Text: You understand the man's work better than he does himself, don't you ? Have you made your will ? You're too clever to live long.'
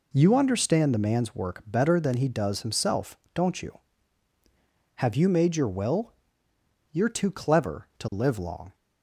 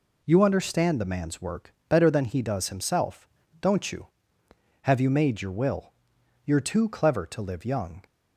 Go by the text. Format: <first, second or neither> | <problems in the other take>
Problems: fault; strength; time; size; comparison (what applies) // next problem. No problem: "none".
first | says "young" for "long"; at 7.6 s